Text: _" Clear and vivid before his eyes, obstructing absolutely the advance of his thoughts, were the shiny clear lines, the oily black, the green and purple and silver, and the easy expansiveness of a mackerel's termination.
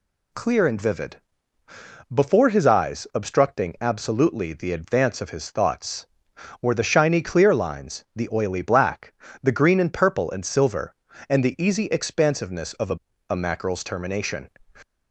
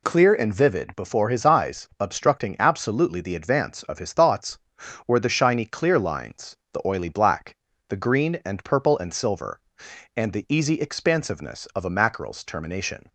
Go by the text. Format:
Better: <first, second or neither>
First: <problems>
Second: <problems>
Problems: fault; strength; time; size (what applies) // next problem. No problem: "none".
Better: second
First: pauses between "vivid" and "before"; noticeable; at 1.2 s; 0.90 s long // says "a" twice; at 13.2 s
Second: none